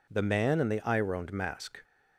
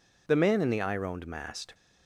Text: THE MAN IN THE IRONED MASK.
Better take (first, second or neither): first